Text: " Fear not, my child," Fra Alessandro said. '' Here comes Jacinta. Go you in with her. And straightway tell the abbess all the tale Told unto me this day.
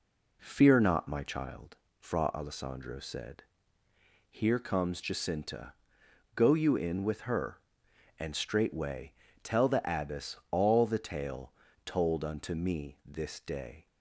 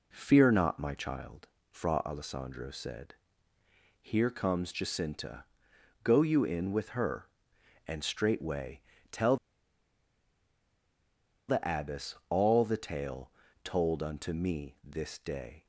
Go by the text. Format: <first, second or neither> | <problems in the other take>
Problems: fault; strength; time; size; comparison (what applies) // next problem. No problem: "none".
first | pauses between "straightway" and "tell"; slight; at 8.8 s; 0.28 s long; slight in the first // pauses between "tell" and "the"; strong; at 9.3 s; 2.1 s long // pauses between "abbess" and "all"; slight; at 12.1 s; 0.16 s long; slight in the first // pauses between "tale" and "Told"; slight; at 13.3 s; 0.32 s long; slight in the first